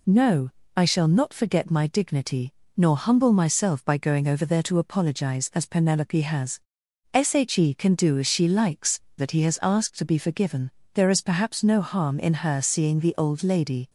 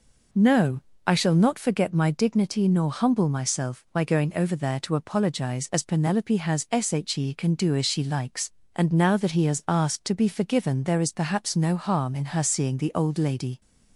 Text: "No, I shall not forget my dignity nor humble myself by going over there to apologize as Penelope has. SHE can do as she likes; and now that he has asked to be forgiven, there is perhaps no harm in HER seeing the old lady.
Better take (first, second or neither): second